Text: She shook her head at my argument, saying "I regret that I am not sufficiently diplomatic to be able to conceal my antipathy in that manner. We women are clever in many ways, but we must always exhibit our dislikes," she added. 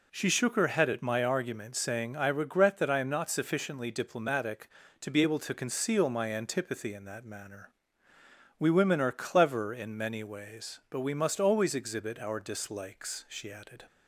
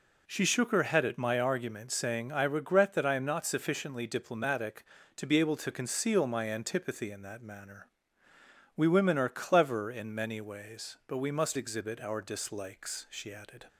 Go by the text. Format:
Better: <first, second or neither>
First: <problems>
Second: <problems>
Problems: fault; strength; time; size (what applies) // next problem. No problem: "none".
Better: first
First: none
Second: skips "always"; at 11.5 s